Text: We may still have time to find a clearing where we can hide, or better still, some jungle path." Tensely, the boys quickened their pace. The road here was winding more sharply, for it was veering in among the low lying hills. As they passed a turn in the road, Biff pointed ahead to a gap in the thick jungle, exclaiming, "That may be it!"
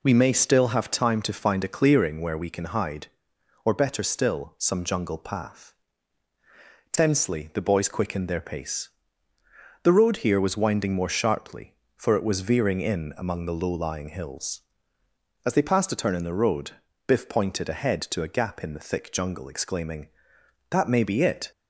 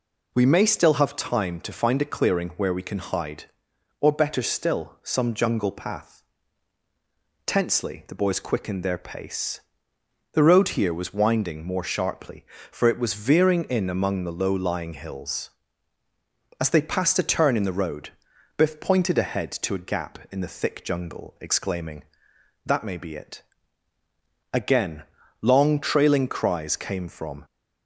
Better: first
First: none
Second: goes on to say "Again long trailing cries came from"; strong; from 24.5 s on; 2.9 s long

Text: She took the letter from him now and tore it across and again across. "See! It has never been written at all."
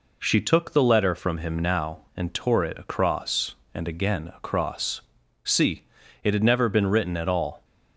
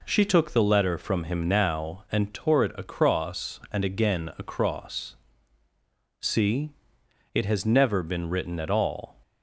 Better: second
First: says "had" for "has"; at 6.3 s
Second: none

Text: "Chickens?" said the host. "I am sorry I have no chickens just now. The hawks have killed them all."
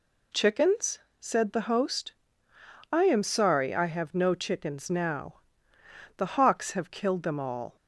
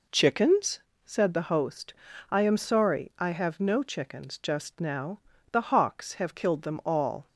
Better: second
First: skips "just"; at 4.8 s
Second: none

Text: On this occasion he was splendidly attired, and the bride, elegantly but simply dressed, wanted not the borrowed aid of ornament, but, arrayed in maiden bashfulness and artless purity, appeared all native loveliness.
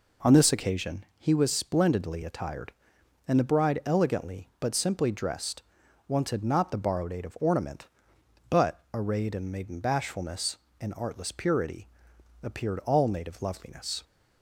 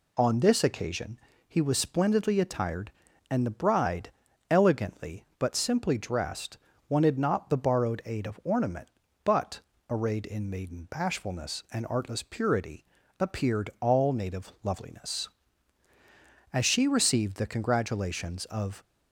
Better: first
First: none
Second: pauses between "occasion" and "he"; slight; at 1.1 s; 0.30 s long // goes on to say "As she received the congratulations of"; strong; from 16.5 s on; 2.3 s long

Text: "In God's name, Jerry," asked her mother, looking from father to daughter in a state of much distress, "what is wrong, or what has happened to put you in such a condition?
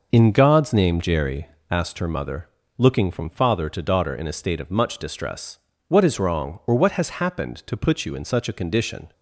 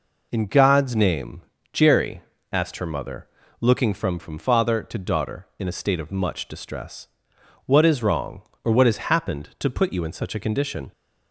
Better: first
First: none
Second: says "from" twice; at 4.1 s

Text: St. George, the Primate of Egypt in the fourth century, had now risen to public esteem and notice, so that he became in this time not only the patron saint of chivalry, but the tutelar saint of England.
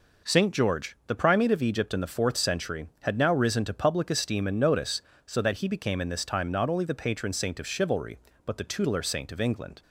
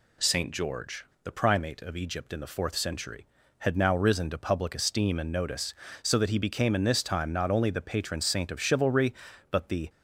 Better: first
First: none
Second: stops before "tutelar saint of England"; at 9.8 s

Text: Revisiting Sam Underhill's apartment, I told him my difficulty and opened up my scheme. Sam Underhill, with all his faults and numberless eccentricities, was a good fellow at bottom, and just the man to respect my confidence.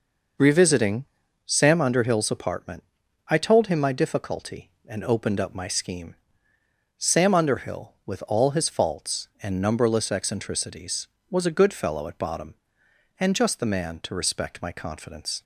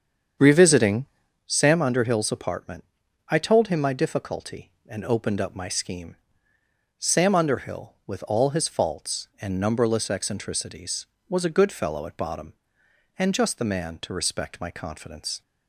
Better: first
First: pauses between "Revisiting" and "Sam"; at 1.0 s; 0.40 s long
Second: starts louder than the rest; strong; until 1.4 s; 7.5 dB // pauses between "Revisiting" and "Sam"; at 1.0 s; 0.40 s long

